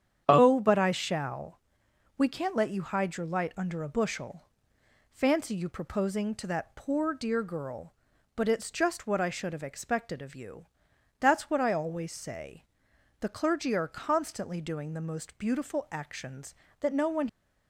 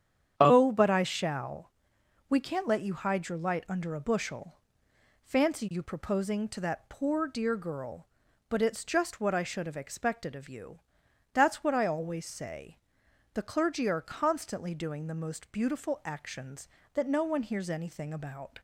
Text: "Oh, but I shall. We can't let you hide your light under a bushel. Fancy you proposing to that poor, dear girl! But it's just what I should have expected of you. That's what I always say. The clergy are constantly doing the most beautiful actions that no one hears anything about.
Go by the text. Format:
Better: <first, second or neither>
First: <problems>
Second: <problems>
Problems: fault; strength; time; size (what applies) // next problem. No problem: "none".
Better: second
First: starts louder than the rest; strong; until 1.2 s; 9 dB // stops before "hears anything about"; at 17.2 s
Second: starts louder than the rest; strong; until 1.3 s; 9 dB